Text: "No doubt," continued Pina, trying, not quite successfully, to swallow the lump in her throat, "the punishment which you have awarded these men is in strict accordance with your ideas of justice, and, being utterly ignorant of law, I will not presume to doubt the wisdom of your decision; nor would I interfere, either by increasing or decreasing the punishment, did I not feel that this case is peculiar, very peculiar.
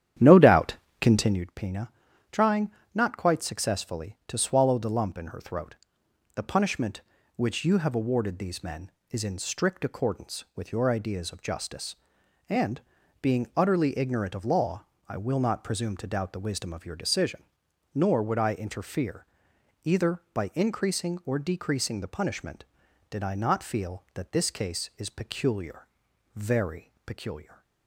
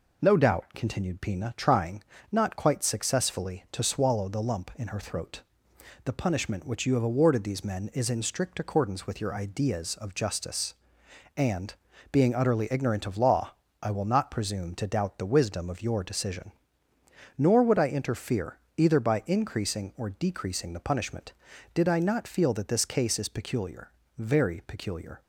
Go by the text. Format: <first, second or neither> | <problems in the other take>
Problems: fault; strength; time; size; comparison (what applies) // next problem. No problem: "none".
second | starts louder than the rest; strong; until 1.5 s; 10.5 dB